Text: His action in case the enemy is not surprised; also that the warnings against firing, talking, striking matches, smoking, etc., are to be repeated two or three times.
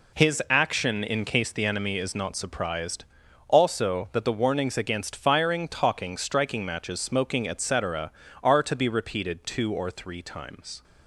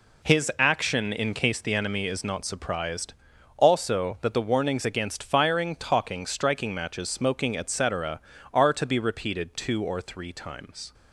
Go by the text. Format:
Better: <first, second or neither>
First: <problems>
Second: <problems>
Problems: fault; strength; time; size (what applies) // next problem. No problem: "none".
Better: neither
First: none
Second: none